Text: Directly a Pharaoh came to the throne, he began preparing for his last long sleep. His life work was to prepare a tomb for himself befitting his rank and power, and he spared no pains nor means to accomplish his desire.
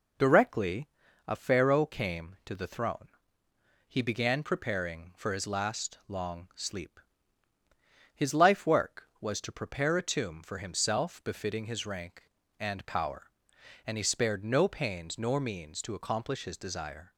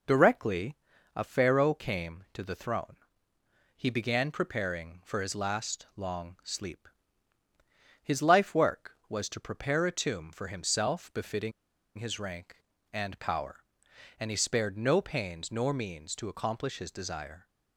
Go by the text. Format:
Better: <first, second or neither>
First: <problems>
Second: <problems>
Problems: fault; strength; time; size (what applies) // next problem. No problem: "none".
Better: first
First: pauses between "Directly" and "a"; at 0.8 s; 0.40 s long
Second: pauses between "Directly" and "a"; at 0.7 s; 0.40 s long // pauses between "befitting" and "his"; at 11.5 s; 0.45 s long